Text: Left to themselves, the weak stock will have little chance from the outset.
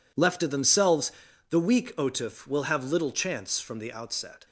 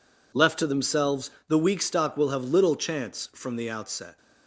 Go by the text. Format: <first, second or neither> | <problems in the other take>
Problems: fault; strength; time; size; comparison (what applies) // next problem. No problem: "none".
second | says "otif" for "stock"; at 1.9 s